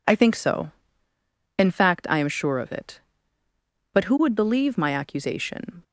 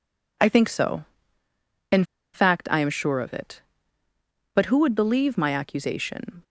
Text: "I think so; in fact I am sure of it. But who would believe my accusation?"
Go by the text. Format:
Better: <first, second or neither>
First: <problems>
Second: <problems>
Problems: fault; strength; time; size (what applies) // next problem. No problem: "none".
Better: first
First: none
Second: pauses between "in" and "fact"; slight; at 2.0 s; 0.28 s long